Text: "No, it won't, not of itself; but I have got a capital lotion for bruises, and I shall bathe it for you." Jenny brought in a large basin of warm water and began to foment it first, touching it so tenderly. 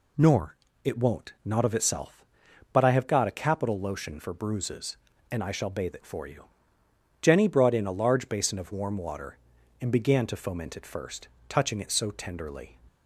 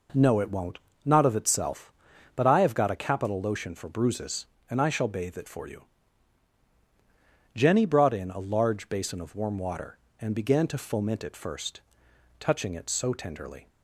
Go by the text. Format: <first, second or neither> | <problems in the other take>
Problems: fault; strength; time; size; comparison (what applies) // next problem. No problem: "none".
second | says "Nor" for "No"; at 0.1 s